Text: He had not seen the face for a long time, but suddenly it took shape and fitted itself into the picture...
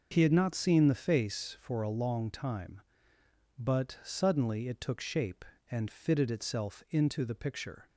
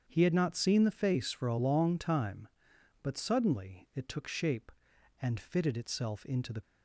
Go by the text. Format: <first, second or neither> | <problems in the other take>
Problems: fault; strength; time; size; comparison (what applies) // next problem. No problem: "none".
first | starts louder than the rest; strong; until 1.1 s; 7.5 dB // stops before "picture"; at 6.6 s